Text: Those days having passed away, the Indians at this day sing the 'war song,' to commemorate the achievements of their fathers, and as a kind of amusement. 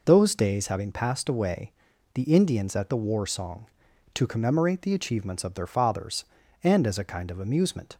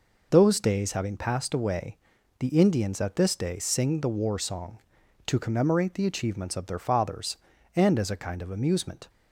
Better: second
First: skips "this day sing"; at 2.9 s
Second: none

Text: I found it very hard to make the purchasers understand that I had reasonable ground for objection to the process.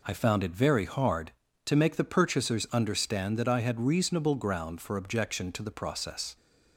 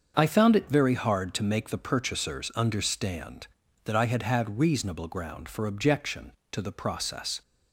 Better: first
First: none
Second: starts louder than the rest; until 1.1 s; 6.5 dB // says "had" twice; at 4.2 s

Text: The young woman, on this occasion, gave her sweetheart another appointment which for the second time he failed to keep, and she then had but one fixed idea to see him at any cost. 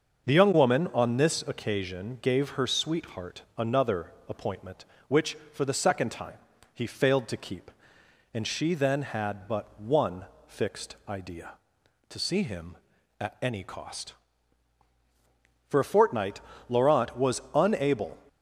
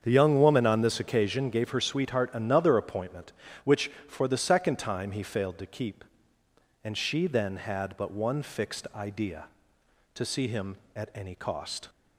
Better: second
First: starts louder than the rest; until 1.3 s; 6 dB // pauses between "sweetheart" and "another"; slight; at 3.4 s; 0.16 s long // pauses between "another" and "appointment"; slight; at 4.1 s; 0.16 s long // pauses between "time" and "he"; slight; at 6.3 s; 0.36 s long // pauses between "one" and "fixed"; slight; at 10.2 s; 0.22 s long // goes on to say "For a fortnight Laurent was unable"; strong; from 15.6 s on; 2.5 s long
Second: starts louder than the rest; strong; until 1.0 s; 7.5 dB

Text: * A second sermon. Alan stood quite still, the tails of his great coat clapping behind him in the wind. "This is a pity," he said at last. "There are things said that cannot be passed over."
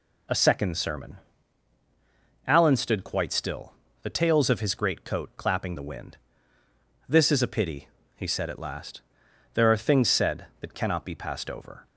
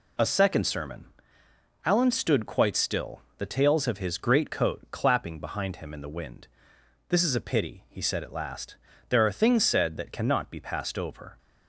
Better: second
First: skips "behind him in"; at 5.7 s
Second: none

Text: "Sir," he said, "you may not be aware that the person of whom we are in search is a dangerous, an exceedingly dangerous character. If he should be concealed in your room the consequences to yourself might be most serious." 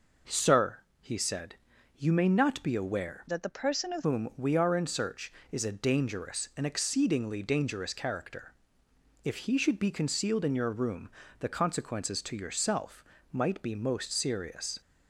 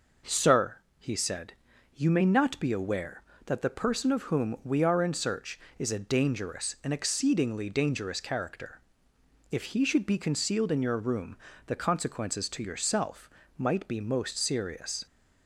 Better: second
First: changes voice from "that" to "of"; from 3.2 to 4.0 s; 0.8 s long // pauses between "room" and "the"; slight; at 11.0 s; 0.30 s long // pauses between "yourself" and "might"; slight; at 13.0 s; 0.26 s long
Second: pauses between "room" and "the"; slight; at 11.3 s; 0.30 s long // pauses between "yourself" and "might"; slight; at 13.3 s; 0.26 s long

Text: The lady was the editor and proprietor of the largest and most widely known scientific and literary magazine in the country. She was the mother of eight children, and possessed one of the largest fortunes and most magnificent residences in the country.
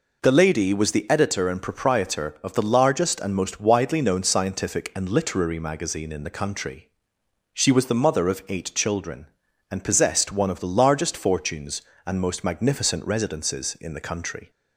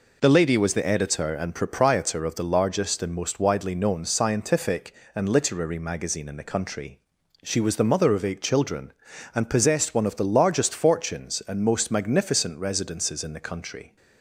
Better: neither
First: none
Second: none

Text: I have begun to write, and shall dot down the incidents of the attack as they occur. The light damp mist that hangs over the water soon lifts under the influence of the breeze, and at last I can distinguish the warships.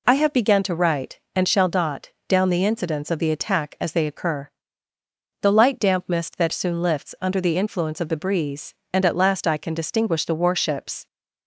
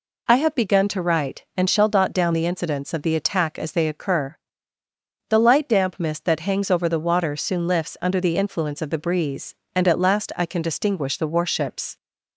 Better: second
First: pauses between "dot" and "down"; slight; at 2.0 s; 0.18 s long // skips "hangs over the water"; at 6.5 s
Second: none

